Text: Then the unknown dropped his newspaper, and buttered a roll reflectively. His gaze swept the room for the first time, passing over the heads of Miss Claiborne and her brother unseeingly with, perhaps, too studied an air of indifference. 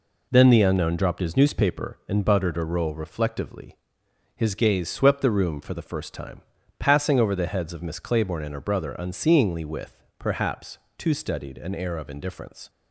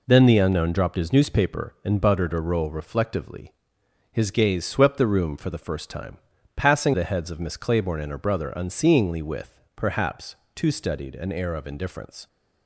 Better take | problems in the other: first | skips "over"; at 6.9 s

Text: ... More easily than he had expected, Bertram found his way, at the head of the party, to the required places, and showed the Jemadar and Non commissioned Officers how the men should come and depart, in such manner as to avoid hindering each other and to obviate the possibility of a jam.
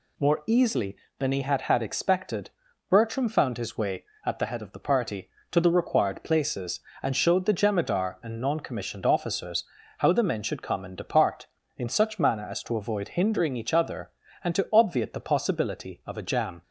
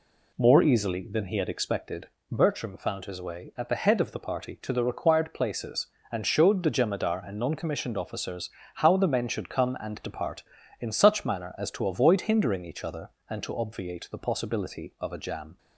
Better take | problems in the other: second | says "had" twice; at 1.6 s // pauses between "Officers" and "how"; slight; at 9.6 s; 0.34 s long; slight in the second

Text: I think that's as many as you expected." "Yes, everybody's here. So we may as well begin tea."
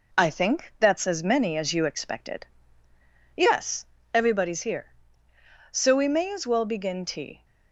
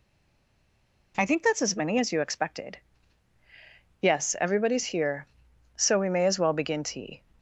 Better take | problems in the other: first | stays silent before the first word; until 1.1 s; 1.1 s long

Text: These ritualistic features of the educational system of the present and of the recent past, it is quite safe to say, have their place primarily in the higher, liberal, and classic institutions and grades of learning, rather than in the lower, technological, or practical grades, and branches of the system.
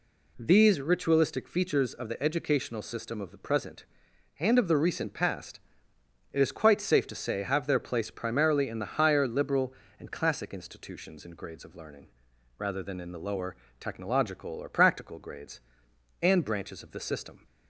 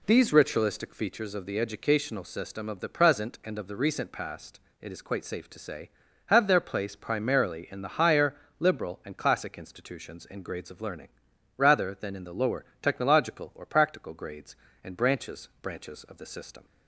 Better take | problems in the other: first | says "branches" twice; at 15.6 s

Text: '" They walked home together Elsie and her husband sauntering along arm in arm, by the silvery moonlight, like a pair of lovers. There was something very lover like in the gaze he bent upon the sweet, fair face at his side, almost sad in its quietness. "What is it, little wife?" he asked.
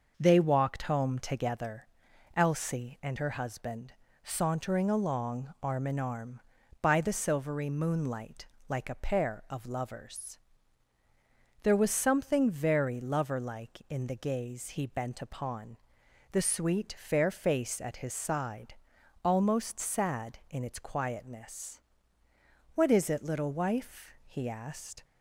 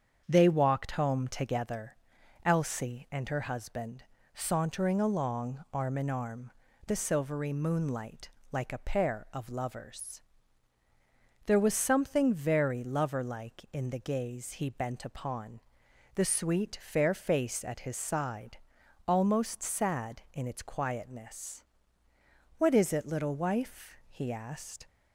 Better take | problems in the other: first | starts louder than the rest; strong; until 1.2 s; 7.5 dB // pauses between "together" and "Elsie"; noticeable; at 1.9 s; 0.50 s long; noticeable in the first // pauses between "husband" and "sauntering"; slight; at 4.0 s; 0.30 s long; slight in the first // skips "by"; at 6.6 s // pauses between "upon" and "the"; noticeable; at 15.6 s; 0.54 s long; noticeable in the first

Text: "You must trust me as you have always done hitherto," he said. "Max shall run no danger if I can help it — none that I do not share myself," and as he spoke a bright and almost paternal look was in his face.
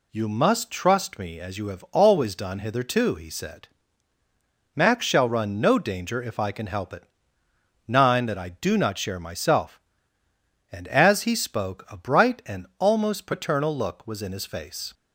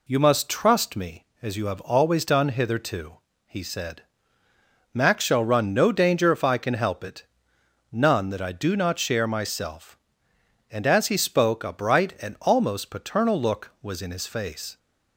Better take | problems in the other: second | says "nine" for "none"; at 7.8 s

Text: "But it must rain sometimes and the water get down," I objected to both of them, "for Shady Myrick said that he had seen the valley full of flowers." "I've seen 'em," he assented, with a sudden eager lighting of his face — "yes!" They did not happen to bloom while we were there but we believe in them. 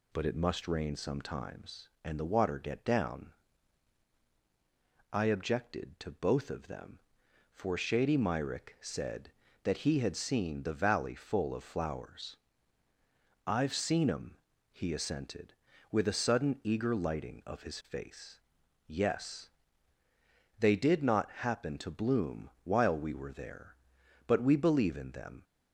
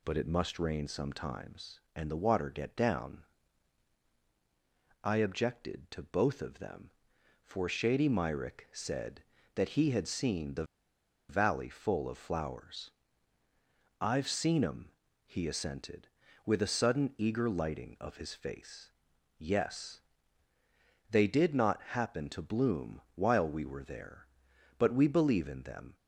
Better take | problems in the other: first | pauses between "the" and "valley"; noticeable; at 10.6 s; 0.65 s long

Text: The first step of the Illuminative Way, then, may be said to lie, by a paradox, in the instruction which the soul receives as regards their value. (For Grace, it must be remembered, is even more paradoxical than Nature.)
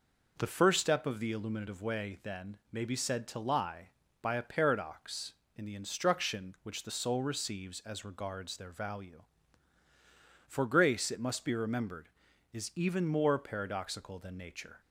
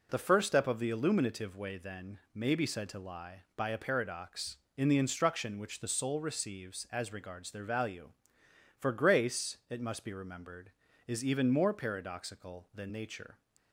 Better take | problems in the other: neither | none

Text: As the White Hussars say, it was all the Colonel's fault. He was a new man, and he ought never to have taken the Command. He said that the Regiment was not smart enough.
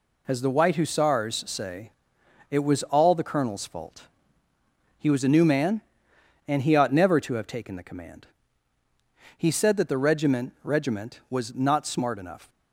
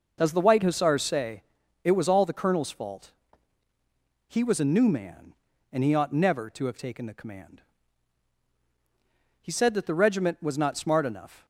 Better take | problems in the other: second | says "Regiment" twice; at 10.6 s

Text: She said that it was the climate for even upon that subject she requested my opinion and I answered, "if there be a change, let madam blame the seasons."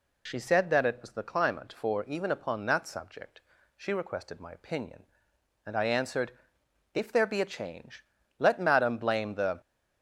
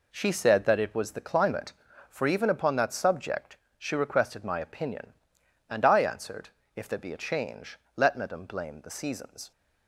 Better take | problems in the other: second | pauses between "subject" and "she"; slight; at 3.4 s; 0.36 s long; slight in the second // stops before "seasons"; at 9.6 s

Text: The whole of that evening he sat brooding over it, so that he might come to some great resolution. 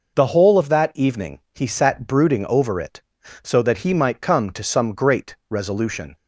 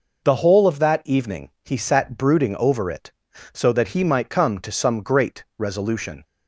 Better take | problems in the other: neither | pauses between "evening" and "he"; slight; the same in both

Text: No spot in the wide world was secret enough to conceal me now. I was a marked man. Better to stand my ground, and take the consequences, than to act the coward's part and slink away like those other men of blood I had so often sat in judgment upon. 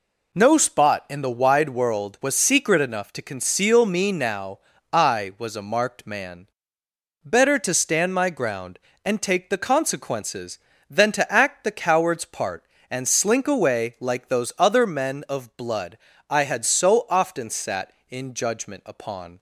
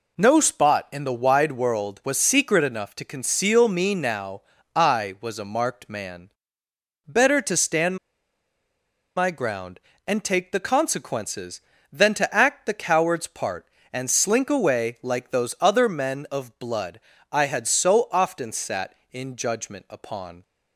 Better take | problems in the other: first | pauses between "stand" and "my"; at 7.9 s; 1.1 s long // pauses between "blood" and "I"; slight; at 16.9 s; 0.32 s long; slight in the first

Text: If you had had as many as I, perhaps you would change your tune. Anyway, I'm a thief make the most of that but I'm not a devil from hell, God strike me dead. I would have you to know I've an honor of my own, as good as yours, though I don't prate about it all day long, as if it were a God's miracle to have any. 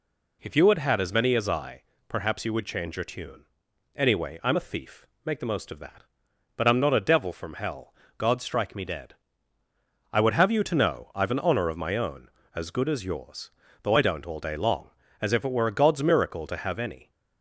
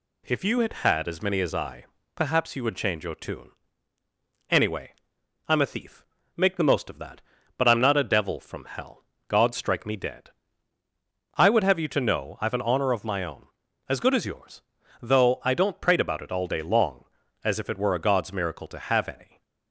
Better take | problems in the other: second | pauses between "thief" and "make"; slight; at 5.0 s; 0.20 s long; slight in the second // skips "prate about it"; at 14.2 s

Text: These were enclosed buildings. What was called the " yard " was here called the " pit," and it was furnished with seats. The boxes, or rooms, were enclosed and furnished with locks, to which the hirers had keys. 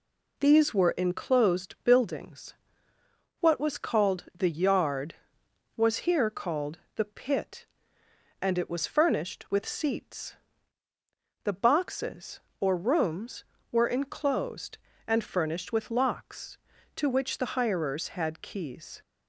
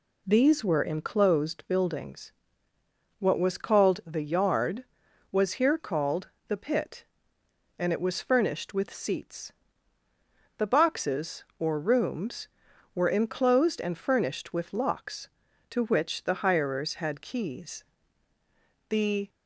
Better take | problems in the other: first | pauses between "called" and "the"; slight; at 6.2 s; 0.18 s long; slight in the first // goes on to say "The"; slight; from 18.8 s on; 0.40 s long

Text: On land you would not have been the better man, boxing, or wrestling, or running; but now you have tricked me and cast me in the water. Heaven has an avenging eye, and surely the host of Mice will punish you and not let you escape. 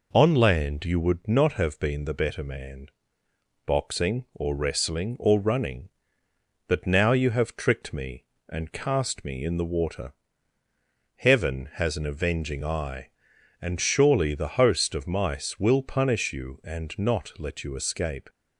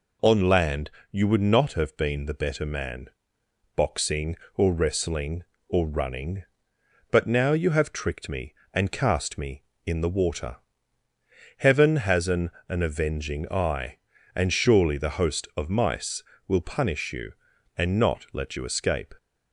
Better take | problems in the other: first | pauses between "land" and "you"; slight; at 0.8 s; 0.22 s long // says "an" twice; at 12.6 s

